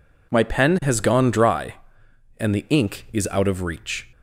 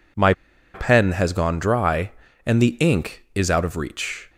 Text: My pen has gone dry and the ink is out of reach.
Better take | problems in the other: first | pauses between "My" and "pen"; at 0.3 s; 0.42 s long

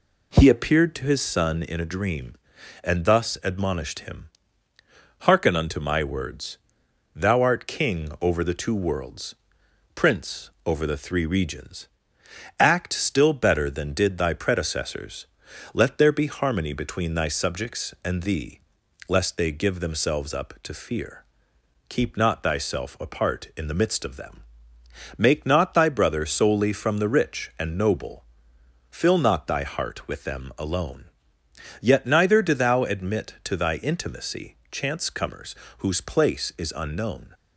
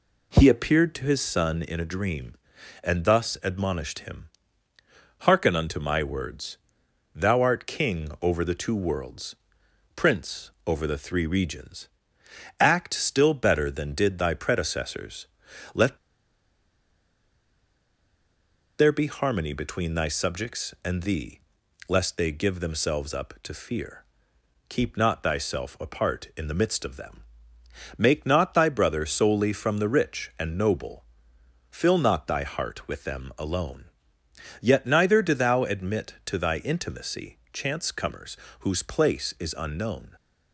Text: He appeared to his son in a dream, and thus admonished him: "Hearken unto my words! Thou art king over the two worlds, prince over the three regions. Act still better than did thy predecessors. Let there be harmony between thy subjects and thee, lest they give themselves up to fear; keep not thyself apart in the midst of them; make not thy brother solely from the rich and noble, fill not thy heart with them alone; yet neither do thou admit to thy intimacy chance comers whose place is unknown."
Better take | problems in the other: first | pauses between "prince" and "over"; slight; at 10.4 s; 0.16 s long; slight in the first // pauses between "Let" and "there"; strong; at 15.9 s; 2.8 s long // pauses between "comers" and "whose"; slight; at 38.3 s; 0.22 s long; slight in the first

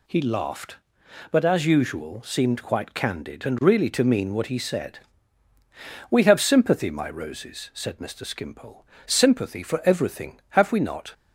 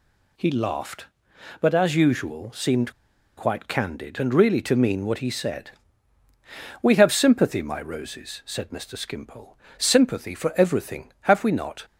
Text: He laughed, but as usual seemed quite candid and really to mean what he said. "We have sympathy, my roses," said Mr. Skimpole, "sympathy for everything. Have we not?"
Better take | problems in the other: first | pauses between "seemed" and "quite"; at 2.9 s; 0.44 s long

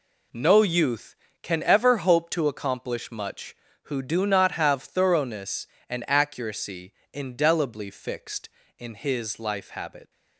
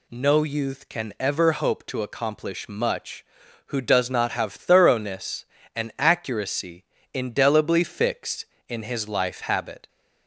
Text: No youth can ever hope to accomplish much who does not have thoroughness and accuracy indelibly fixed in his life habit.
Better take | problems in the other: second | says "do" for "does"; at 4.0 s // pauses between "accuracy" and "indelibly"; slight; at 6.9 s; 0.20 s long; slight in the second

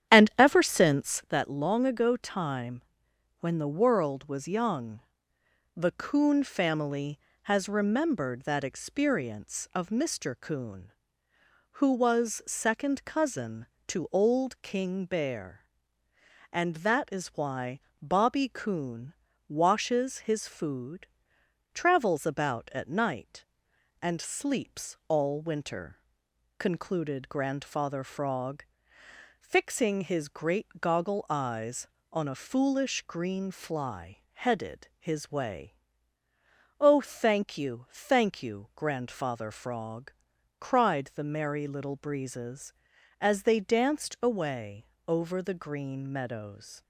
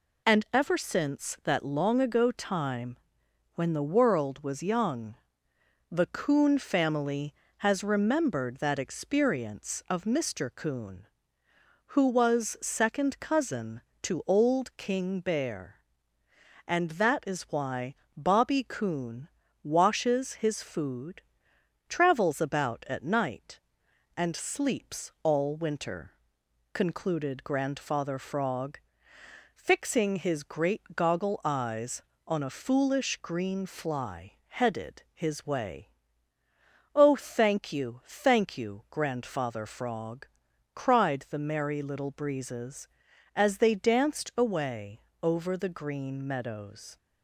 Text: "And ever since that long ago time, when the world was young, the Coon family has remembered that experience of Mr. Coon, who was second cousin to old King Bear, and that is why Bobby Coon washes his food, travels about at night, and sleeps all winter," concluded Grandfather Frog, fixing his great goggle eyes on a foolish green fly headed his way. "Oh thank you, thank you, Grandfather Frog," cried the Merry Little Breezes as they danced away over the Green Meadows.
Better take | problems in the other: second | starts louder than the rest; strong; until 1.4 s; 10 dB // pauses between "why" and "Bobby"; slight; at 17.8 s; 0.20 s long; slight in the second // pauses between "Coon" and "washes"; slight; at 19.1 s; 0.36 s long; slight in the second // pauses between "away" and "over"; slight; at 44.8 s; 0.22 s long; slight in the second

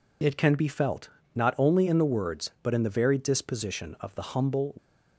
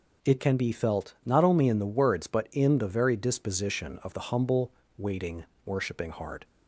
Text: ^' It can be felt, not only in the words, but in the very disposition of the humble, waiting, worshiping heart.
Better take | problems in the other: second | stops before "waiting worshiping heart"; at 4.7 s

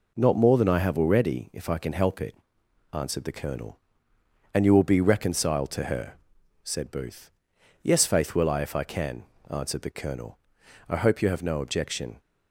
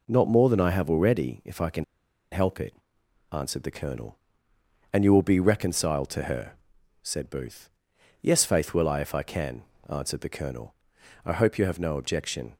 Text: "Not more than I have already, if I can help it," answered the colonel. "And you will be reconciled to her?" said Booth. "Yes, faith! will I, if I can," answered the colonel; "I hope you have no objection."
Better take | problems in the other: first | pauses between "can" and "help"; noticeable; at 1.8 s; 0.47 s long

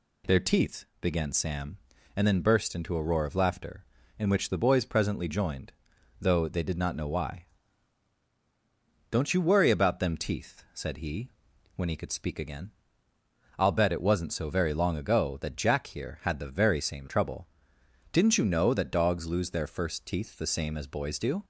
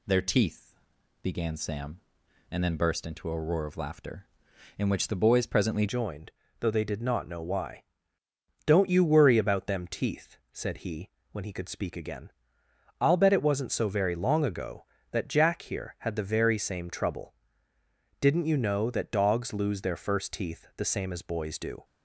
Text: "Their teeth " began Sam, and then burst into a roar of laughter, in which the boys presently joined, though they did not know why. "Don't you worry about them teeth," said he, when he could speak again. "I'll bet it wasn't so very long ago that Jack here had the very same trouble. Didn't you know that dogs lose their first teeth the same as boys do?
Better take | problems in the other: first | changes voice at "joined"; from 5.8 s on; 16.0 s long

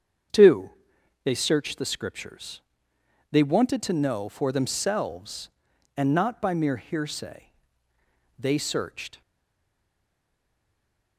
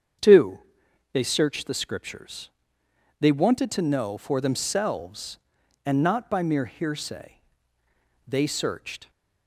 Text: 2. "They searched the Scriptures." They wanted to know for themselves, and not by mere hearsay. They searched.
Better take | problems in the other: second | starts louder than the rest; strong; until 1.8 s; 7.5 dB; strong in the second // stays silent after the last word; noticeable; from 9.2 s on; 1.9 s long

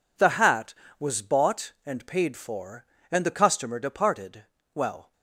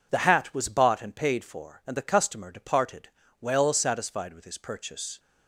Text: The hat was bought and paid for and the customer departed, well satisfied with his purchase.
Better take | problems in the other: second | stops before "satisfied with his purchase"; at 5.1 s

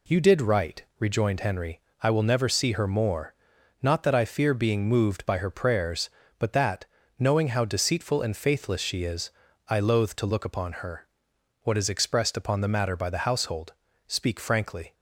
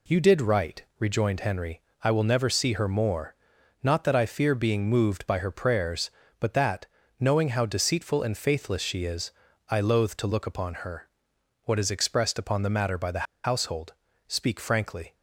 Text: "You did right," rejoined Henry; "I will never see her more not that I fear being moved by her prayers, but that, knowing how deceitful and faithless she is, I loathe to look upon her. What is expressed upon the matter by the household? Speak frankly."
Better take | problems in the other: first | pauses between "more" and "not"; noticeable; at 3.3 s; 0.48 s long; noticeable in the first // pauses between "the" and "household"; slight; at 13.2 s; 0.19 s long

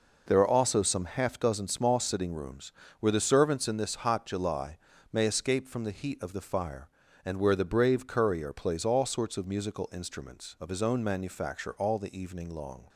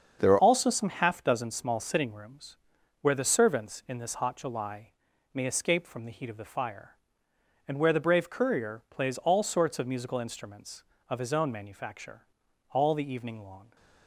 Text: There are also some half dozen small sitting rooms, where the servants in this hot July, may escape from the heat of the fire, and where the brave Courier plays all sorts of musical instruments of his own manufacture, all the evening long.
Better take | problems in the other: first | starts louder than the rest; until 1.2 s; 7 dB // changes voice at "also"; from 0.3 s on; 13.4 s long

